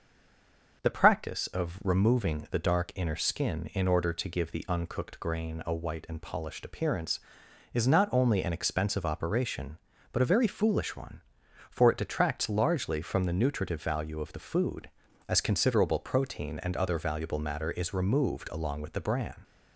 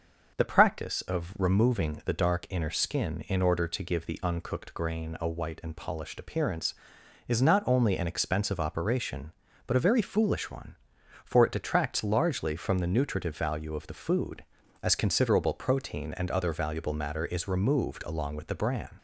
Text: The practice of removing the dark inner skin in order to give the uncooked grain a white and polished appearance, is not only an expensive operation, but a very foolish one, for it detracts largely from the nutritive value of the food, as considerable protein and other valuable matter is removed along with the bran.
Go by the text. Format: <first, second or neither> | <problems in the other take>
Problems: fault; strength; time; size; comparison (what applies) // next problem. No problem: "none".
second | stays silent before the first word; slight; until 0.8 s; 0.8 s long // starts louder than the rest; until 1.8 s; 6.5 dB; also in the second